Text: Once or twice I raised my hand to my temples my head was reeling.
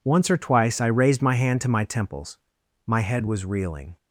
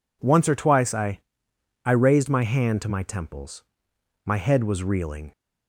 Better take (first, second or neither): first